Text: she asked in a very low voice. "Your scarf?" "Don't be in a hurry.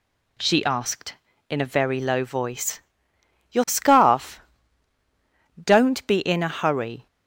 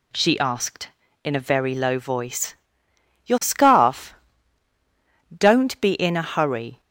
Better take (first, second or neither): neither